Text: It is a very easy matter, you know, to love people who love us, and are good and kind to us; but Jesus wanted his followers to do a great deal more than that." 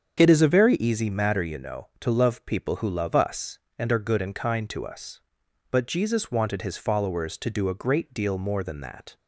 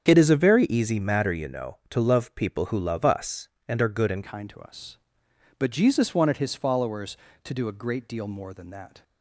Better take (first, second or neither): first